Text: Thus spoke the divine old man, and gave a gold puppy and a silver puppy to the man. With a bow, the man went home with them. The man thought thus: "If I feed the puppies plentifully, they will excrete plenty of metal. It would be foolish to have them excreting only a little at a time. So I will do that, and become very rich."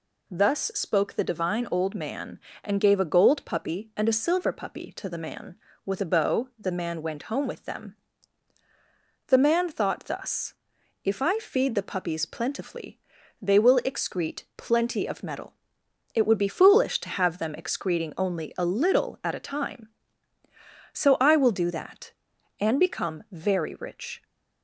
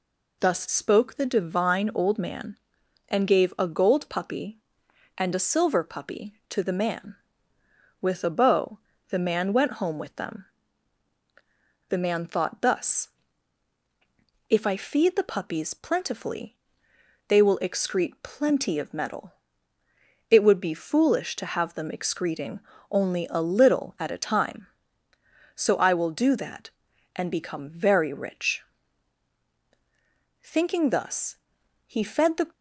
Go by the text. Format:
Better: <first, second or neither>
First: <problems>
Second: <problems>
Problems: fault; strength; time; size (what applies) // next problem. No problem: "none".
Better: first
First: none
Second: pauses between "excreting" and "only"; slight; at 22.6 s; 0.30 s long // goes on to say "Thinking thus he fed the"; strong; from 30.4 s on; 2.1 s long